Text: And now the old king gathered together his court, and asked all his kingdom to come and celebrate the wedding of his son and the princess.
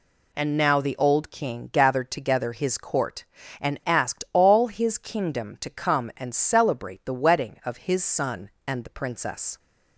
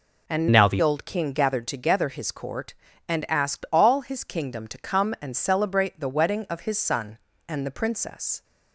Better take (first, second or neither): first